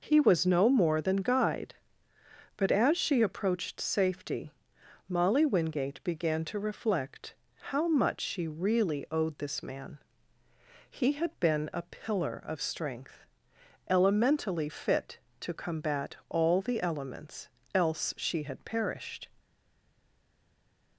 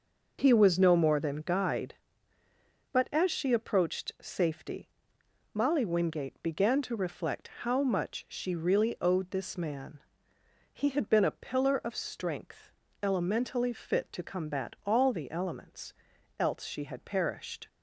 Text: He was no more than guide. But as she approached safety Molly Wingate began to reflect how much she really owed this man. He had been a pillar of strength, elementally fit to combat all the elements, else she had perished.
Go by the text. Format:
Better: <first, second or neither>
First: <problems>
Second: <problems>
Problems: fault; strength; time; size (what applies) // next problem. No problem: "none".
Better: second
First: pauses between "safety" and "Molly"; noticeable; at 4.5 s; 0.56 s long // pauses between "reflect" and "how"; slight; at 7.3 s; 0.34 s long // stays silent after the last word; noticeable; from 19.3 s on; 1.6 s long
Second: pauses between "safety" and "Molly"; noticeable; at 4.8 s; 0.64 s long // pauses between "reflect" and "how"; slight; at 7.4 s; 0.16 s long